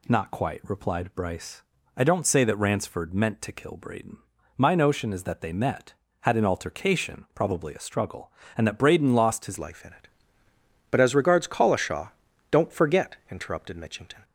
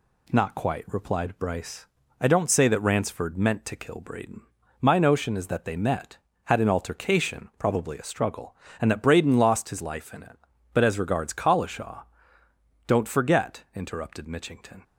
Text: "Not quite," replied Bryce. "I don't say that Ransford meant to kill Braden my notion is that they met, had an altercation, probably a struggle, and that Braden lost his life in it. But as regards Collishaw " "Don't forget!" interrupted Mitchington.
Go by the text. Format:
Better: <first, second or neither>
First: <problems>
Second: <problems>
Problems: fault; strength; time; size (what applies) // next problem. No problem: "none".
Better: second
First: pauses between "Braden" and "my"; at 4.1 s; 0.38 s long // changes voice at "life"; from 9.5 s on; 4.7 s long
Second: pauses between "Braden" and "my"; at 4.4 s; 0.38 s long